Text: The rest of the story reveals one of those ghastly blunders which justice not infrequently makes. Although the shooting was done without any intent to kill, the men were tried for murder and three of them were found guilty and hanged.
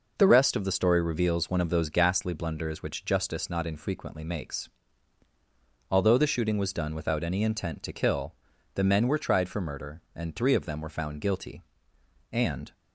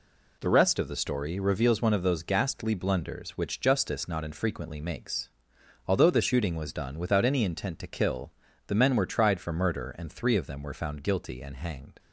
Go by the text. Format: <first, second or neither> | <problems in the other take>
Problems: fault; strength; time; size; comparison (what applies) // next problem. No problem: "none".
second | stops before "hanged"; at 12.7 s